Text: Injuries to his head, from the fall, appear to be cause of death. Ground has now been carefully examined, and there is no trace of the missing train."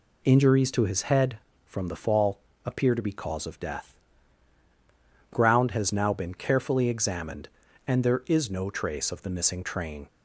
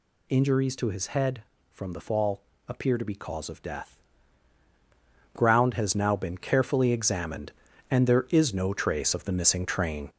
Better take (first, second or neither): first